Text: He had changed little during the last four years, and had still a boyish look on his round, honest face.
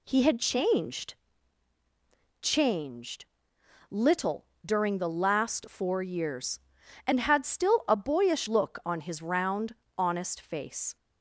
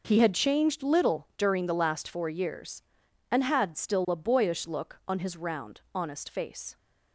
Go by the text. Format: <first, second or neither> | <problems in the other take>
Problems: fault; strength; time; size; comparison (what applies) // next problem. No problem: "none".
second | says "changed" twice; at 2.4 s // pauses between "little" and "during"; slight; at 4.4 s; 0.18 s long